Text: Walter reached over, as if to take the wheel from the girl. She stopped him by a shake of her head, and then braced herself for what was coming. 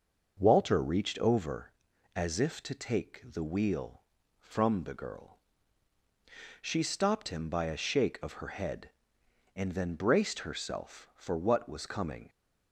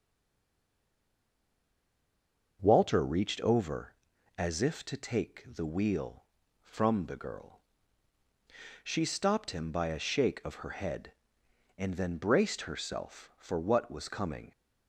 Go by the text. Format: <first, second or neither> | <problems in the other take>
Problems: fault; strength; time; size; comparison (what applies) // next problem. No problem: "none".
first | stays silent before the first word; strong; until 2.5 s; 2.5 s long // starts louder than the rest; until 3.6 s; 6.5 dB; also in the first